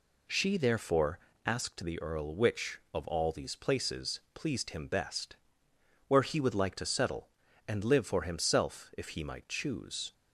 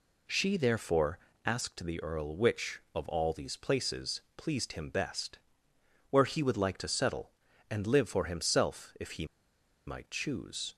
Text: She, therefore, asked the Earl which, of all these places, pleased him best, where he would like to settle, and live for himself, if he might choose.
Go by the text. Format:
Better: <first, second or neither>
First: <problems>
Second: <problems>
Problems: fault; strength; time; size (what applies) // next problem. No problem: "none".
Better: first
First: none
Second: pauses between "he" and "might"; noticeable; at 9.2 s; 0.61 s long